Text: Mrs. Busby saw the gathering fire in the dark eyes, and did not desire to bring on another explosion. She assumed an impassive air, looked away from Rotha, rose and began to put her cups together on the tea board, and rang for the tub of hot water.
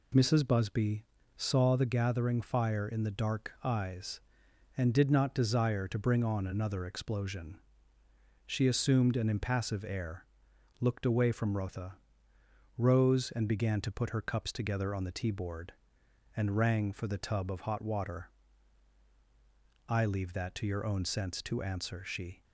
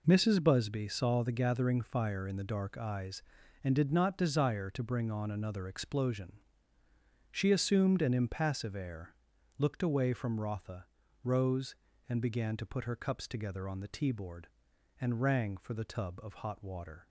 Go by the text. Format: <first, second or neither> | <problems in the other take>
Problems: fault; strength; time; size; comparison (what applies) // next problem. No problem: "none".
second | pauses between "Busby" and "saw"; slight; at 1.0 s; 0.30 s long // goes on to say "I leave that to your own sense to answer she"; strong; from 19.8 s on; 2.5 s long